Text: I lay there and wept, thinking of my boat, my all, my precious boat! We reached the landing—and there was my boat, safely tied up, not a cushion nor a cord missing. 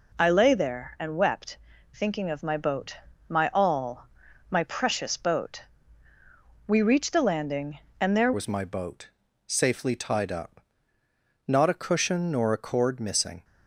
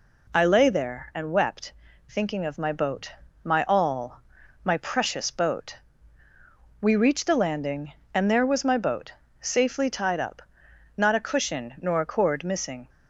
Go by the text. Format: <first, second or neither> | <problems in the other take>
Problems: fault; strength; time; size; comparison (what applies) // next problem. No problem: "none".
second | changes voice at "was"; from 8.3 s on; 5.1 s long